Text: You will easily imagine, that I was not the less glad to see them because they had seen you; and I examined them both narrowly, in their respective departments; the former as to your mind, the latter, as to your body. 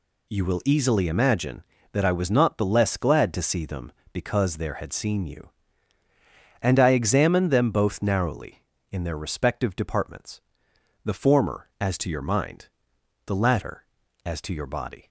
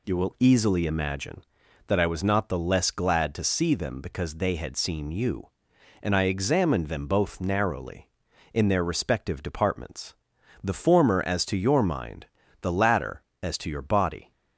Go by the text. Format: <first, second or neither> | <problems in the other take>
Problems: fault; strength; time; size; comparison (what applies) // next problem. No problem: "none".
second | says "there" for "they"; at 4.5 s